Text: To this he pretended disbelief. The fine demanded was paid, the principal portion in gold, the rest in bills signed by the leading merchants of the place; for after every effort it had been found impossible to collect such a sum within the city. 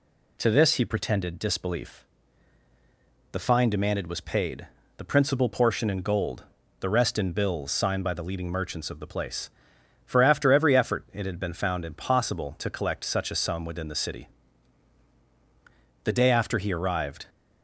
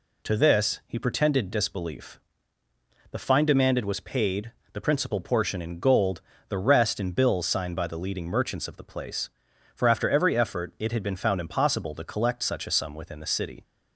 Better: second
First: goes on to say "The day after he arrived"; noticeable; from 16.0 s on; 1.2 s long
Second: none

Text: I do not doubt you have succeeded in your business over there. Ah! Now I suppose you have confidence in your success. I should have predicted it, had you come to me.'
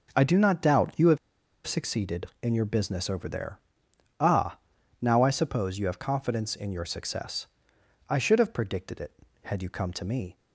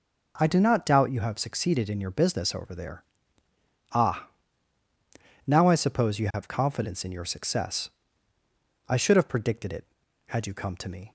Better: second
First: pauses between "have" and "succeeded"; noticeable; at 1.1 s; 0.49 s long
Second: none

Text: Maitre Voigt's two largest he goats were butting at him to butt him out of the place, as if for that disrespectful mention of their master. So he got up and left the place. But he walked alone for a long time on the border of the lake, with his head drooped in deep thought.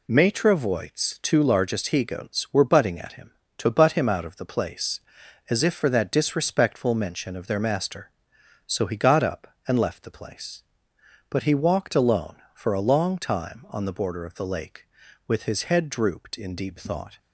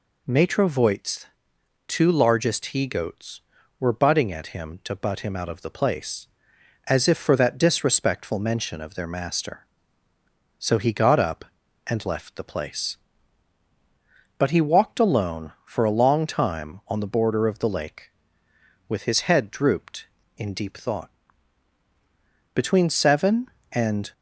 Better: first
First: none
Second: pauses between "Voigt's" and "two"; noticeable; at 1.2 s; 0.60 s long // goes on to say "Between seven and"; from 22.5 s on; 1.5 s long

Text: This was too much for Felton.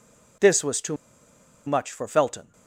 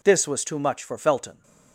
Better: second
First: pauses between "too" and "much"; noticeable; at 0.9 s; 0.70 s long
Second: none

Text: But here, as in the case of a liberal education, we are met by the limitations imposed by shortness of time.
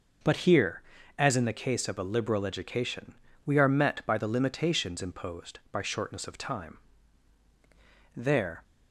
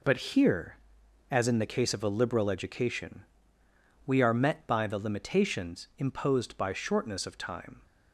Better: second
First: goes on to say "There"; slight; from 8.1 s on; 0.48 s long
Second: none

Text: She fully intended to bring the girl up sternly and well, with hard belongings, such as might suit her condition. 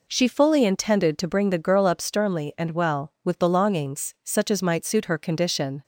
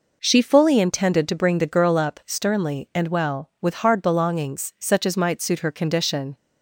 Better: second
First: skips "hard"; at 3.3 s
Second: none

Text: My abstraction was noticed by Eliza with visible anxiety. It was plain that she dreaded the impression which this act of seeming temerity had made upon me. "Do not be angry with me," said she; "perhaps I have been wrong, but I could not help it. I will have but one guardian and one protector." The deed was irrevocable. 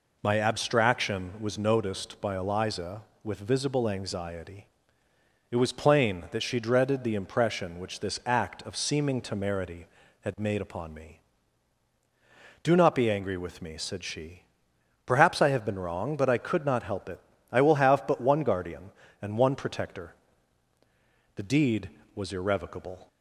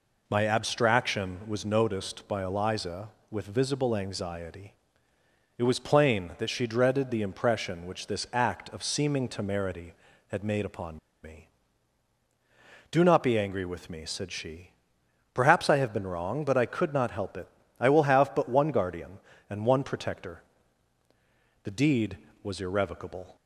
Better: first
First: none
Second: pauses between "upon" and "me"; slight; at 10.9 s; 0.25 s long

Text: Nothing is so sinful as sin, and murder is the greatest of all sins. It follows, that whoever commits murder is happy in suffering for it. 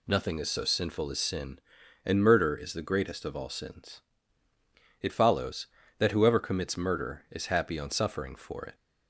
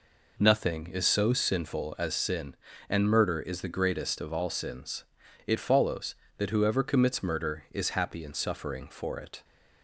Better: second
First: says "on" for "in"; at 7.7 s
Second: none

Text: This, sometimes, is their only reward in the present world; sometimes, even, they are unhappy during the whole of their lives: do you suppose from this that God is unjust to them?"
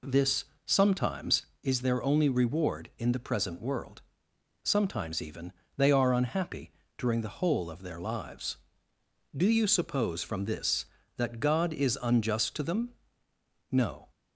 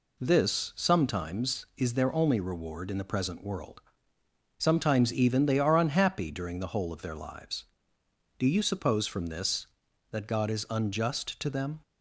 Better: second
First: pauses between "unhappy" and "during"; slight; at 6.7 s; 0.26 s long // goes on to say "No"; slight; from 13.7 s on; 0.38 s long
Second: none

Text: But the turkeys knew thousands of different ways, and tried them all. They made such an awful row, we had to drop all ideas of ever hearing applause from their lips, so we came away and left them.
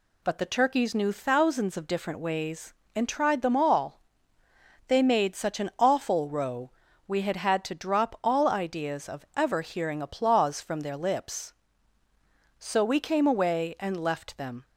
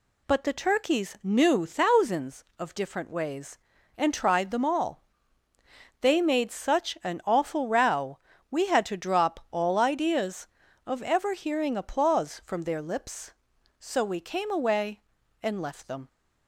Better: second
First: says "had" twice; at 7.3 s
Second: none

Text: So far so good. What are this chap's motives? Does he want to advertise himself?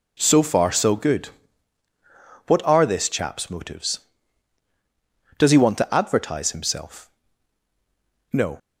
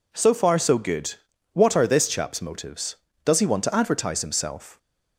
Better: second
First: goes on to say "No"; slight; from 8.3 s on; 0.26 s long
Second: none

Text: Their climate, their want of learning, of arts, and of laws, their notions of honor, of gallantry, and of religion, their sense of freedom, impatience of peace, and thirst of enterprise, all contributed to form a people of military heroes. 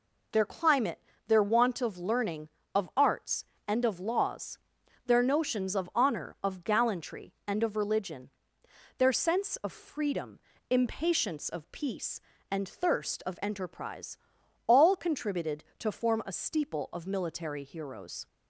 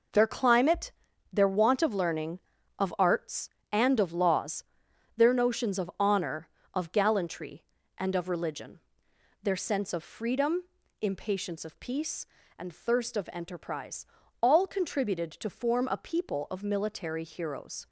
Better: second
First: says "steeple" for "people"; at 16.3 s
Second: none

